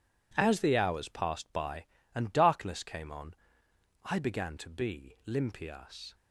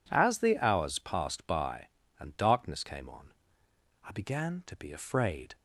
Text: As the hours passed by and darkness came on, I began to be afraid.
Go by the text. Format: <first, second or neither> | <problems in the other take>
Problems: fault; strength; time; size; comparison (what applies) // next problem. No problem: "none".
second | says "limpias" for "afraid"; at 5.2 s